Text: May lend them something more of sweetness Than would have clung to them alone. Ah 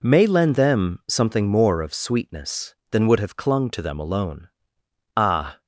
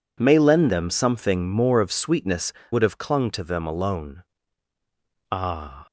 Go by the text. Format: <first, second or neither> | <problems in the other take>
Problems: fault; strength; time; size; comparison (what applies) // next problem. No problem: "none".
first | skips "Than"; at 2.6 s